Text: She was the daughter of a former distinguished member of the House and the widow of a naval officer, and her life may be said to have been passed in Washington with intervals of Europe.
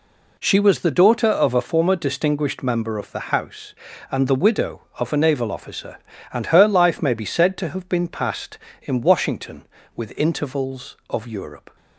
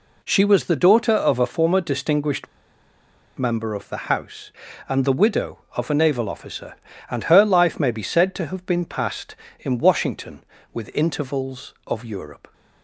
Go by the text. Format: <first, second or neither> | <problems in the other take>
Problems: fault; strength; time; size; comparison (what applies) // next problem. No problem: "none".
first | pauses between "distinguished" and "member"; noticeable; at 2.4 s; 0.92 s long